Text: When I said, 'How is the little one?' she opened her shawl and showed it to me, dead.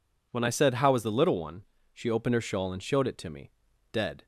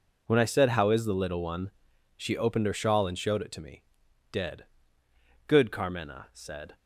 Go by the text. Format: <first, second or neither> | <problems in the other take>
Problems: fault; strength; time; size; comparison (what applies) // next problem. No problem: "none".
first | goes on to say "Good Carmena said"; noticeable; from 5.4 s on; 1.2 s long